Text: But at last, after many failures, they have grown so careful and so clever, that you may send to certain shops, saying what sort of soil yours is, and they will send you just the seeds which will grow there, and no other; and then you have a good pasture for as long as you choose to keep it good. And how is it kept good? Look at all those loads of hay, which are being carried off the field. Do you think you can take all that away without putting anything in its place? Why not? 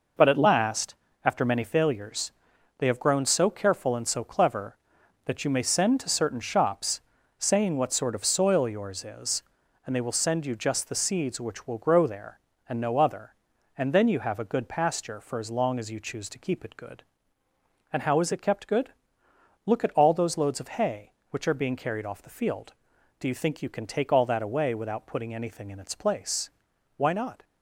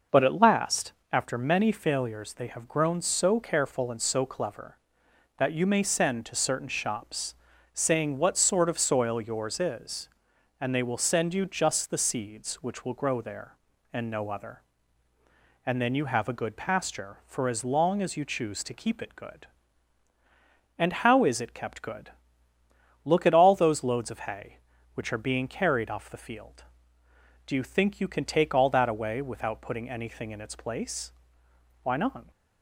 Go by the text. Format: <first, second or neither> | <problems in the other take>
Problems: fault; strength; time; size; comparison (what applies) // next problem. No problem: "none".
neither | none